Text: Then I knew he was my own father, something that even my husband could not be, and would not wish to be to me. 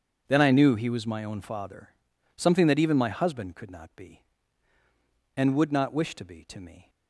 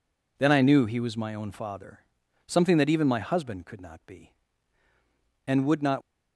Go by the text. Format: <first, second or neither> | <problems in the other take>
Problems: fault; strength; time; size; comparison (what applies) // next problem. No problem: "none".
first | stops before "wish to be to me"; at 6.0 s